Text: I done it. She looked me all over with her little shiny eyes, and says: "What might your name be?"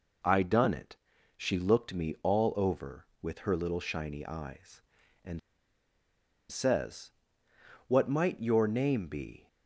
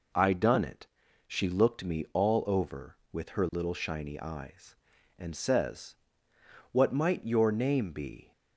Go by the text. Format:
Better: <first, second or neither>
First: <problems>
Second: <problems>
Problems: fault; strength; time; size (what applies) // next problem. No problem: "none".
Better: second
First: pauses between "and" and "says"; at 5.3 s; 1.1 s long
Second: none